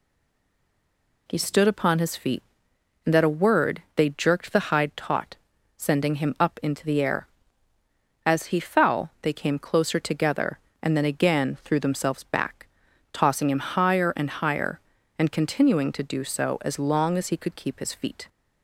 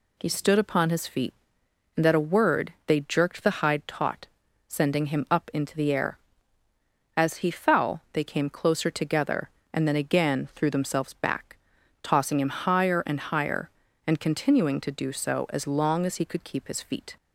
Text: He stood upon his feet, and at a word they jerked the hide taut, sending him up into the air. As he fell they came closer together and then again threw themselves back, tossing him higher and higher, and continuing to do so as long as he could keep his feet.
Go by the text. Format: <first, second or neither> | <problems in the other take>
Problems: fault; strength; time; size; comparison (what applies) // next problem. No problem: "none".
second | stays silent before the first word; noticeable; until 1.2 s; 1.2 s long